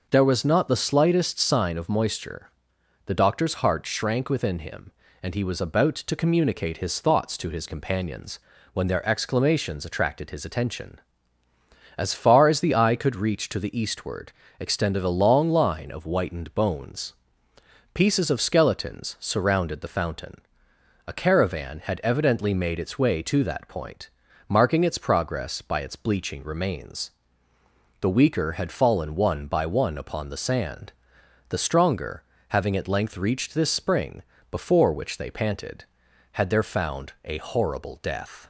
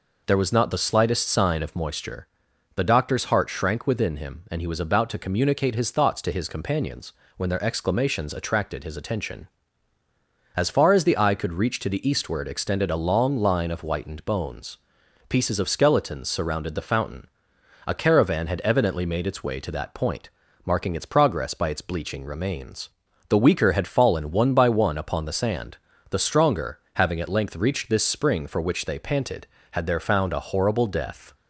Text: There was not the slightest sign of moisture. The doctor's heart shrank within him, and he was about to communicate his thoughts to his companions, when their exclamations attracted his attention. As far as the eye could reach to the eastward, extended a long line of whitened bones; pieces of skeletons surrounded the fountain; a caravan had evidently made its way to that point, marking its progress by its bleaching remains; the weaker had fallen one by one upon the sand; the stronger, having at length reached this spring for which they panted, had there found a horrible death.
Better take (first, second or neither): second